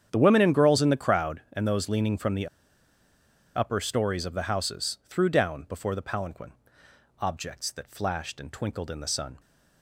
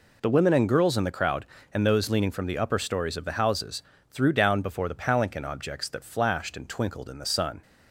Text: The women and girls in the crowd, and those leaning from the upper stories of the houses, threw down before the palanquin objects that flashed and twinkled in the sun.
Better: second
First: starts louder than the rest; strong; until 1.1 s; 8.5 dB // pauses between "the" and "upper"; at 2.4 s; 1.0 s long // pauses between "palanquin" and "objects"; noticeable; at 6.5 s; 0.68 s long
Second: none

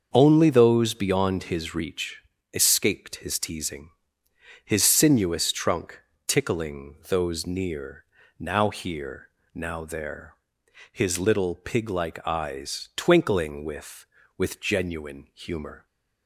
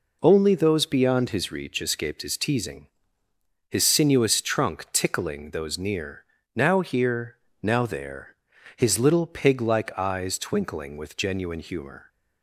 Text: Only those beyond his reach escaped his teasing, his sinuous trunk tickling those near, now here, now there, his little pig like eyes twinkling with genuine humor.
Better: second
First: starts louder than the rest; until 1.1 s; 6.5 dB // pauses between "reach" and "escaped"; slight; at 2.2 s; 0.32 s long // pauses between "trunk" and "tickling"; slight; at 6.0 s; 0.26 s long // says "with" twice; at 14.3 s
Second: none

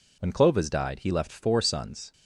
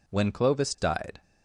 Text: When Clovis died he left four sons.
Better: first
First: none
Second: stops before "he left four sons"; at 1.2 s

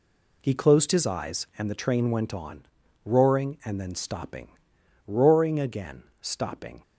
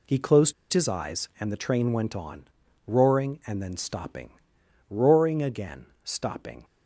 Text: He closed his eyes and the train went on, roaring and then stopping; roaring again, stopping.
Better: first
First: none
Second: pauses between "closed" and "his"; slight; at 0.5 s; 0.19 s long

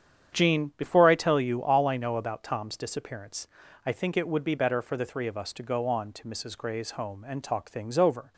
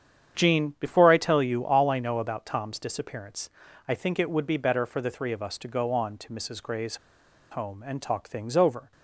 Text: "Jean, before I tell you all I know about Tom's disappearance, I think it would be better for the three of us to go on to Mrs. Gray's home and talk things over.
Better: first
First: starts louder than the rest; strong; until 1.4 s; 8.5 dB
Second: starts louder than the rest; strong; until 1.4 s; 8.5 dB // pauses between "Gray's" and "home"; noticeable; at 6.9 s; 0.55 s long

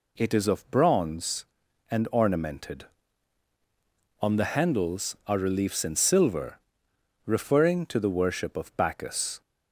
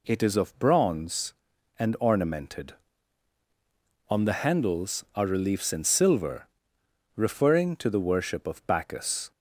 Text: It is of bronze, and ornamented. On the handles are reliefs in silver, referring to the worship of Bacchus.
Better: neither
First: none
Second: none

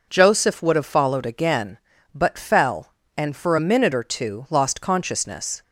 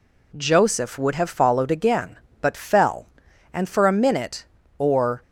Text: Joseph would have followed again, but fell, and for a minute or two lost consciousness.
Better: first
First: none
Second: stops before "two lost consciousness"; at 5.2 s

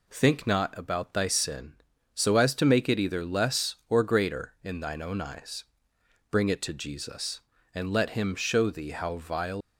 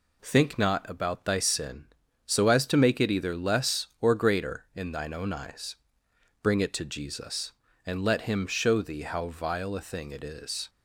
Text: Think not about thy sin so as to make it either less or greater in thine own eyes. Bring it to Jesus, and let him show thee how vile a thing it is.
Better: second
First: stops before "a thing it is"; at 9.6 s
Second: none

